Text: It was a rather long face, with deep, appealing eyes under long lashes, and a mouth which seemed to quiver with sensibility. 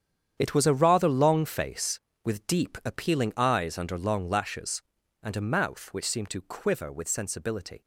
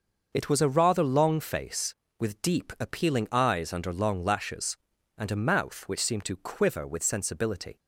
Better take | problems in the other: second | gets quieter; strong; throughout; 12.5 dB // starts louder than the rest; strong; until 1.4 s; 9 dB; also in the second

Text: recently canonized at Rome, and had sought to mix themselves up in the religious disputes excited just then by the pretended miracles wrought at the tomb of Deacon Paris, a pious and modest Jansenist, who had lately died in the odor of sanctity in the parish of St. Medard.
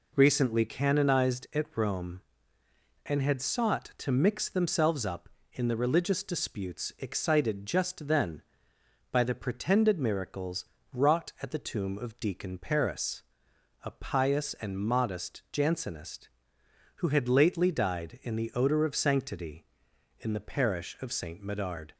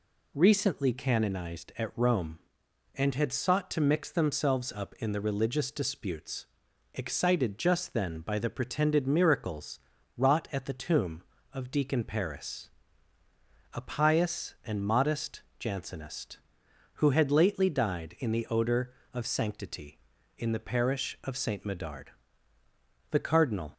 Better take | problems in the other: first | pauses between "disputes" and "excited"; noticeable; at 6.4 s; 0.50 s long // pauses between "miracles" and "wrought"; slight; at 9.7 s; 0.36 s long; slight in the first // pauses between "modest" and "Jansenist"; slight; at 15.4 s; 0.16 s long // goes on to say "The cardinal"; noticeable; from 23.0 s on; 0.64 s long

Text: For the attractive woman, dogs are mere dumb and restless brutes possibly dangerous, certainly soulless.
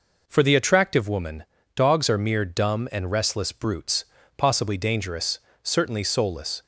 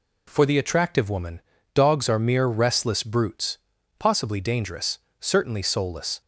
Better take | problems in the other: first | skips "dumb and"; at 2.4 s // pauses between "brutes" and "possibly"; at 3.5 s; 0.42 s long; slight in the first

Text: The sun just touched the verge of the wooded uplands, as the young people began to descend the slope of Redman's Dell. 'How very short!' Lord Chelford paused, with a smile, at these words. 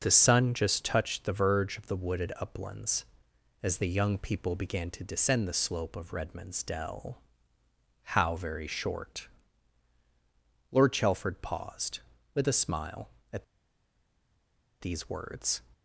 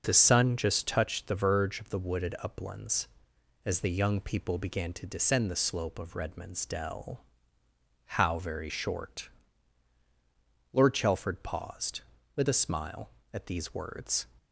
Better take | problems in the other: second | starts louder than the rest; noticeable; until 1.0 s; 6 dB; noticeable in the second // pauses between "at" and "these"; strong; at 13.4 s; 1.3 s long

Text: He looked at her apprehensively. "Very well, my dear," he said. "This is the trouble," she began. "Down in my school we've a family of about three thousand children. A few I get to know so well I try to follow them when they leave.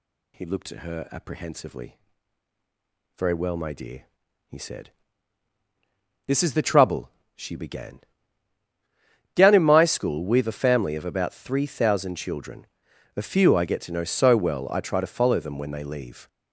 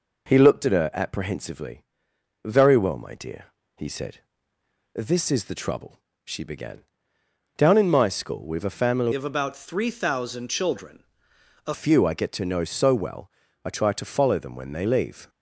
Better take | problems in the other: first | changes voice from "of" to "A"; from 9.1 to 11.7 s; 2.6 s long // pauses between "well" and "I"; slight; at 13.3 s; 0.32 s long

